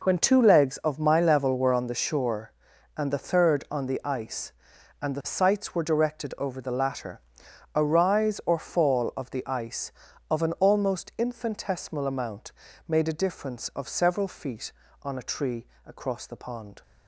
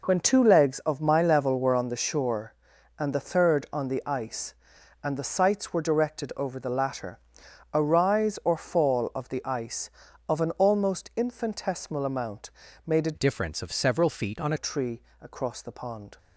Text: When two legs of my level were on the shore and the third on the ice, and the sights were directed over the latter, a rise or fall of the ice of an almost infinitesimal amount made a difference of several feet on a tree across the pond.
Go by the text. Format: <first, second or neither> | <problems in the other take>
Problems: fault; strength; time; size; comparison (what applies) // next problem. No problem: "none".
first | pauses between "amount" and "made"; slight; at 12.5 s; 0.36 s long; slight in the first // changes voice from "difference" to "on"; from 13.1 to 14.5 s; 1.4 s long // pauses between "tree" and "across"; slight; at 15.0 s; 0.20 s long; slight in the first